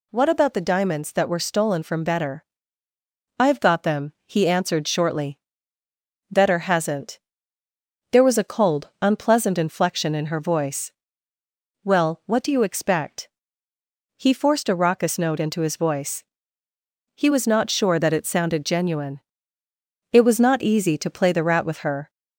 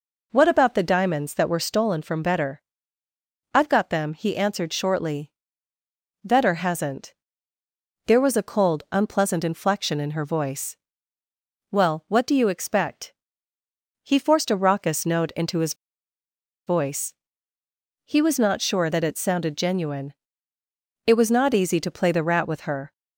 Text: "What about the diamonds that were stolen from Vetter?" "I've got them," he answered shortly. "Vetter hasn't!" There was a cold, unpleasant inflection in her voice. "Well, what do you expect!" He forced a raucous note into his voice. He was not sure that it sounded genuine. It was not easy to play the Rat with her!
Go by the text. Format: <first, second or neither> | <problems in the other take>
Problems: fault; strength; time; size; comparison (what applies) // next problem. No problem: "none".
first | pauses between "his" and "voice"; noticeable; at 15.7 s; 0.92 s long